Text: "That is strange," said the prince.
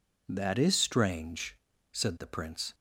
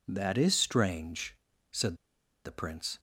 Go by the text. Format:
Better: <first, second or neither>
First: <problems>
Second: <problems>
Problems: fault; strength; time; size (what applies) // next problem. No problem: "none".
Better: first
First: none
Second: pauses between "said" and "the"; noticeable; at 1.9 s; 0.48 s long